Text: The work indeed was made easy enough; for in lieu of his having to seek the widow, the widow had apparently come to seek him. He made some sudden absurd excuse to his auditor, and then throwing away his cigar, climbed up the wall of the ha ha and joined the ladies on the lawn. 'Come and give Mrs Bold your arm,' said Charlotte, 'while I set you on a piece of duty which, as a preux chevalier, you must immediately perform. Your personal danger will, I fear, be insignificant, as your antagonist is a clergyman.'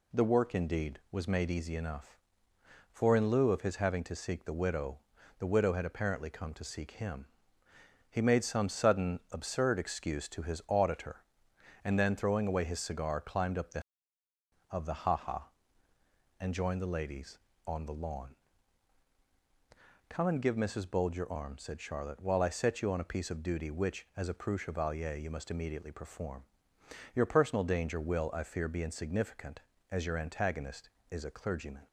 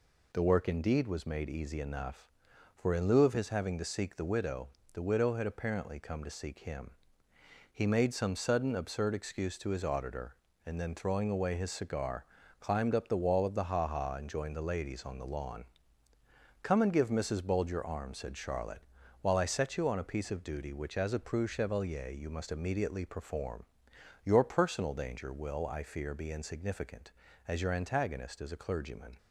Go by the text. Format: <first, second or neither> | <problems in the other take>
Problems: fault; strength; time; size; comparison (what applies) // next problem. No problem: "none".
second | skips "wall"; at 14.2 s